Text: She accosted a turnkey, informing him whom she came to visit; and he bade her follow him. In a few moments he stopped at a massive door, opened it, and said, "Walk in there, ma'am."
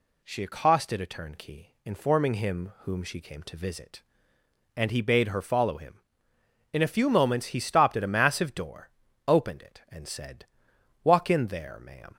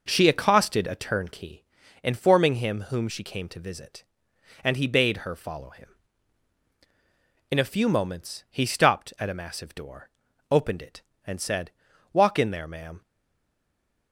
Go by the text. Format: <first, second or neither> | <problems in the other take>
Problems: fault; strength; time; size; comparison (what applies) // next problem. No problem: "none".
first | stays silent after the last word; from 13.0 s on; 1.1 s long